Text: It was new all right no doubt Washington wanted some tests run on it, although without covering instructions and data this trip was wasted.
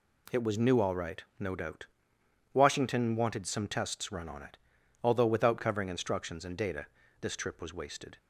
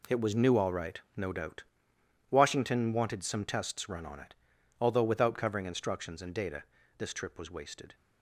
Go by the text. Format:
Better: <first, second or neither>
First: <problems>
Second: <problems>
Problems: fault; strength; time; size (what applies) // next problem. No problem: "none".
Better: first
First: pauses between "doubt" and "Washington"; noticeable; at 1.8 s; 0.66 s long // pauses between "data" and "this"; slight; at 6.8 s; 0.32 s long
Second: gets quieter; strong; throughout; 11 dB // pauses between "doubt" and "Washington"; noticeable; at 1.6 s; 0.66 s long // pauses between "data" and "this"; slight; at 6.6 s; 0.32 s long